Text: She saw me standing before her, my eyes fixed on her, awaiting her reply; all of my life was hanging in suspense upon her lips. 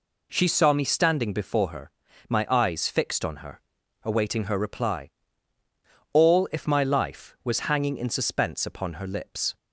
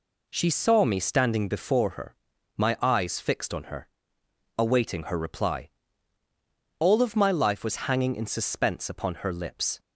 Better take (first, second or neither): second